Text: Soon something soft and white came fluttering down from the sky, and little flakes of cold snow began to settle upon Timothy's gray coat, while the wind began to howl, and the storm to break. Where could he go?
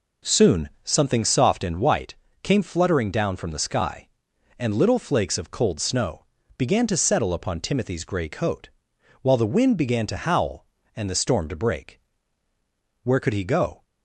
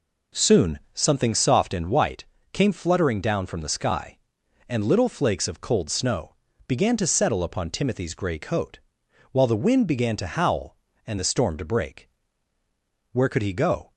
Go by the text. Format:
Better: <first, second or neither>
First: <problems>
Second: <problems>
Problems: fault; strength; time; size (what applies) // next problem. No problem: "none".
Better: neither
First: pauses between "Soon" and "something"; slight; at 0.6 s; 0.16 s long // pauses between "white" and "came"; slight; at 2.1 s; 0.28 s long // pauses between "snow" and "began"; slight; at 6.2 s; 0.32 s long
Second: pauses between "Soon" and "something"; slight; at 0.7 s; 0.16 s long // pauses between "white" and "came"; slight; at 2.2 s; 0.28 s long // pauses between "snow" and "began"; slight; at 6.3 s; 0.32 s long